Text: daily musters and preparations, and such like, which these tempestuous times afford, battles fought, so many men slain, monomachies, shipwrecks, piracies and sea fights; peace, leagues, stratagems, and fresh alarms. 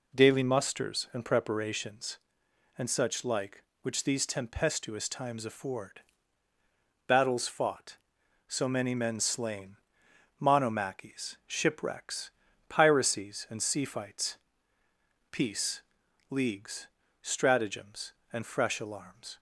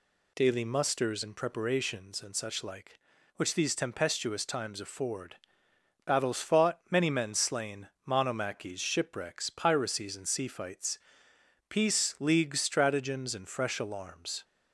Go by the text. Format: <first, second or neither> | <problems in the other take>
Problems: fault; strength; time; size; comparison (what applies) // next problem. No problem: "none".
first | skips "so"; at 6.8 s